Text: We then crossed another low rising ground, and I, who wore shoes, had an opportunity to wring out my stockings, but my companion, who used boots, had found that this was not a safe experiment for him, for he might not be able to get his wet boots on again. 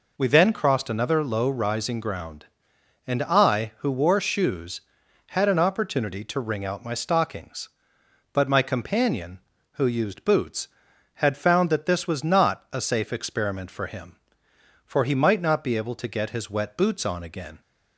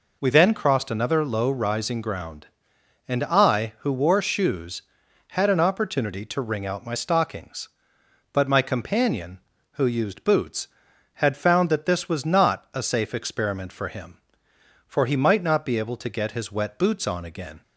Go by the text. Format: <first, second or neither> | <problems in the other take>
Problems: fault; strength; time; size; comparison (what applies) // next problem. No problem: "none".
neither | none